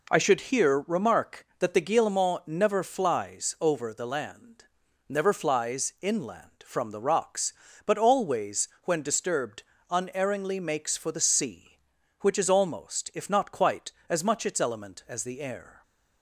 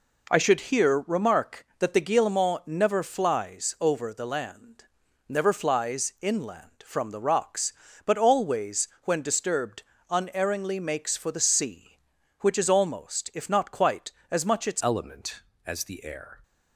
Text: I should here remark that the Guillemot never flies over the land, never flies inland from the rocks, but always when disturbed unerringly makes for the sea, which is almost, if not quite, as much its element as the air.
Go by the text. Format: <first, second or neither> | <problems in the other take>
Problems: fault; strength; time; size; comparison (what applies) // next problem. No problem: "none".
first | pauses between "disturbed" and "unerringly"; slight; at 9.8 s; 0.26 s long; slight in the first // changes voice at "element"; from 14.8 s on; 1.6 s long